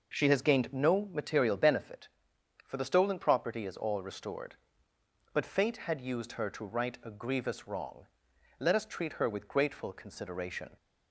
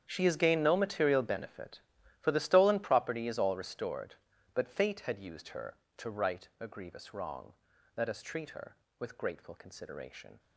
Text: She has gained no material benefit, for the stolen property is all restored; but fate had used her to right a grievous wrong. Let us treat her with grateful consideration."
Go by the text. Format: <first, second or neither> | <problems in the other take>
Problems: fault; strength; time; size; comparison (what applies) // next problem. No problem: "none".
first | gets quieter; strong; throughout; 16 dB